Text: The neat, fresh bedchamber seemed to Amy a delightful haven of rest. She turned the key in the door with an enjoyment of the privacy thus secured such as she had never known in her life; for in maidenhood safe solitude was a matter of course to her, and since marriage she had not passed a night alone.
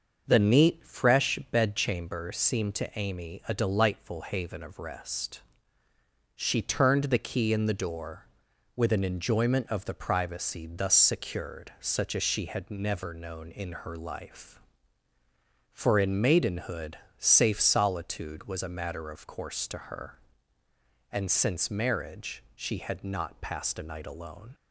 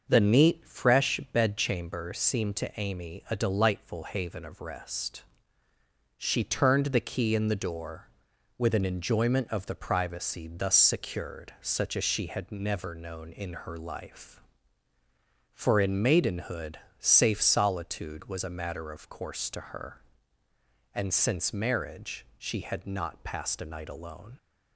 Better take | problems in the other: neither | starts louder than the rest; the same in both // pauses between "maidenhood" and "safe"; slight; the same in both

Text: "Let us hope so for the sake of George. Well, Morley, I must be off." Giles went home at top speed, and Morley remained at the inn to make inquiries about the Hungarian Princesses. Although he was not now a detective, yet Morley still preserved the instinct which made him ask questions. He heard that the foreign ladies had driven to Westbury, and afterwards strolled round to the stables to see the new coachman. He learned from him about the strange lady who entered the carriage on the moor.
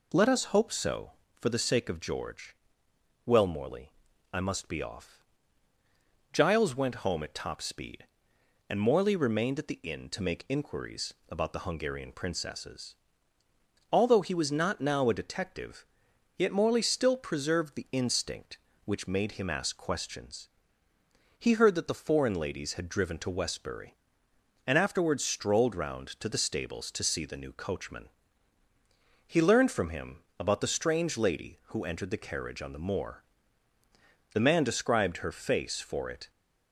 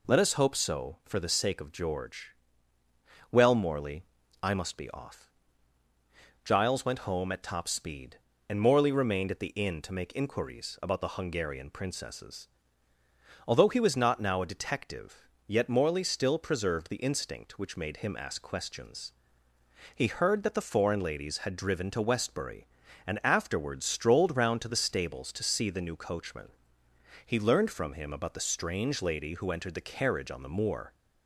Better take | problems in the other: second | pauses between "inquiries" and "about"; slight; at 11.1 s; 0.16 s long // pauses between "him" and "about"; slight; at 30.2 s; 0.16 s long // goes on to say "The man described her face for it"; strong; from 34.3 s on; 1.9 s long

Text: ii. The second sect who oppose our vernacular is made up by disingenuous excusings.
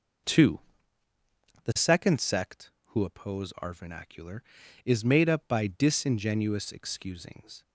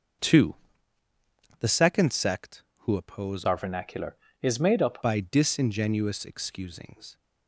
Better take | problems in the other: first | starts louder than the rest; until 2.2 s; 6.5 dB // changes voice from "our" to "up"; from 3.4 to 5.0 s; 1.6 s long

